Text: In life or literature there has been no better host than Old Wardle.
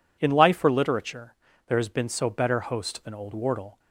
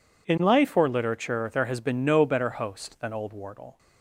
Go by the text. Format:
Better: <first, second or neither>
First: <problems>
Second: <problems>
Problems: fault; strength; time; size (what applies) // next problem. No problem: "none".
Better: second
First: pauses between "literature" and "there"; slight; at 1.3 s; 0.32 s long // says "so" for "no"; at 2.0 s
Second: none